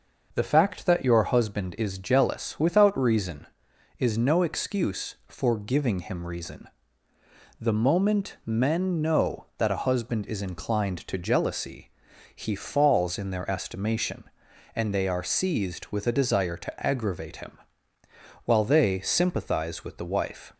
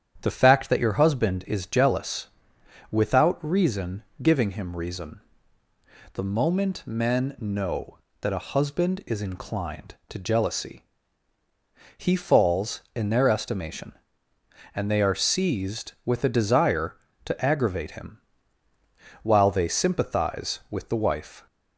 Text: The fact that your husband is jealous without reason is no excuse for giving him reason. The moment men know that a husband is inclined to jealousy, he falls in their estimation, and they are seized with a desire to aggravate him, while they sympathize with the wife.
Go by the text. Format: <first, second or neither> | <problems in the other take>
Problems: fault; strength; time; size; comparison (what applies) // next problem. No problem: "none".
first | starts louder than the rest; strong; until 1.2 s; 9 dB // pauses between "jealous" and "without"; noticeable; at 2.2 s; 0.62 s long // skips "is no excuse for"; at 4.1 s